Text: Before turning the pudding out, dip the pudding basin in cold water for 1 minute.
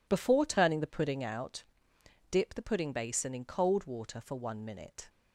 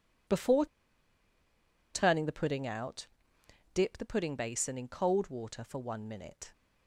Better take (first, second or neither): first